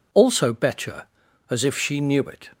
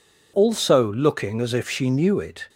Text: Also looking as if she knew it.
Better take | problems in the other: second | says "betcher" for "looking"; at 0.5 s

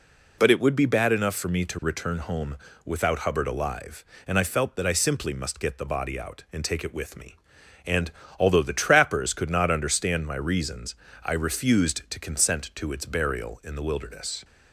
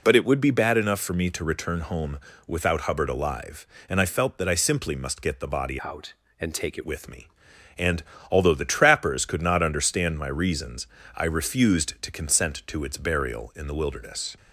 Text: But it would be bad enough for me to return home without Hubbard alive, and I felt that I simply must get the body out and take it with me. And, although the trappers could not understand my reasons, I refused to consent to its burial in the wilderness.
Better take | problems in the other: first | pauses between "home" and "without"; slight; at 2.2 s; 0.26 s long; slight in the first // changes voice from "out" to "it"; from 5.8 to 6.8 s; 1.0 s long

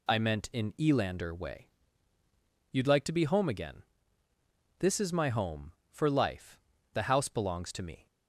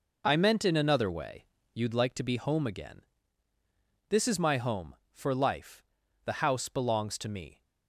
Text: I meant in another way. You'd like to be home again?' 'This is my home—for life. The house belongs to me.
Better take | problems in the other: second | says "elander" for "another"; at 0.7 s

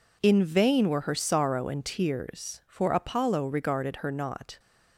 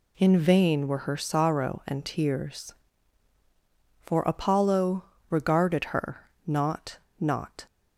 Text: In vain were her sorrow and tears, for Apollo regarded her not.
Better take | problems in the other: first | pauses between "Apollo" and "regarded"; slight; at 5.0 s; 0.26 s long // pauses between "her" and "not"; slight; at 6.2 s; 0.16 s long // says "not" twice; at 7.1 s

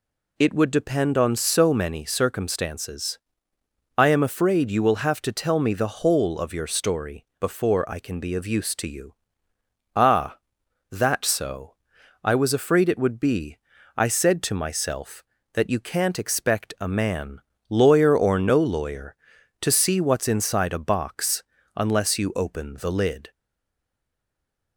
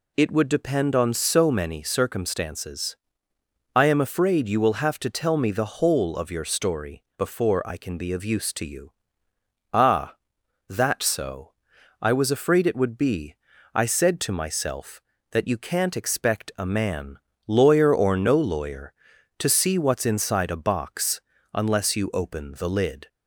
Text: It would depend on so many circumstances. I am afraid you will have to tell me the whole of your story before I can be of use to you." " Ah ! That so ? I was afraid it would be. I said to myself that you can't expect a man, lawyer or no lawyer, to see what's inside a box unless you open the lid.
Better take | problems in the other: second | pauses between "story" and "before"; slight; at 7.2 s; 0.16 s long; slight in the second // pauses between "box" and "unless"; slight; at 21.4 s; 0.34 s long; slight in the second // stays silent after the last word; noticeable; from 23.3 s on; 1.4 s long

